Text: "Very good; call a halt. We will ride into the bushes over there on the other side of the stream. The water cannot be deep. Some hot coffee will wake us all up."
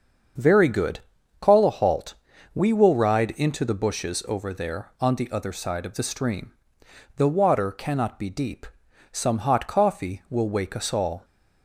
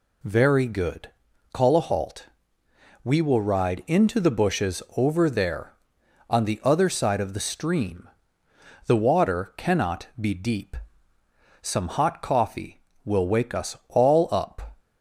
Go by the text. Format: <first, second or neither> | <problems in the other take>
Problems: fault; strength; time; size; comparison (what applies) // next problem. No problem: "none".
second | starts louder than the rest; until 1.7 s; 6.5 dB // stops before "up"; at 11.2 s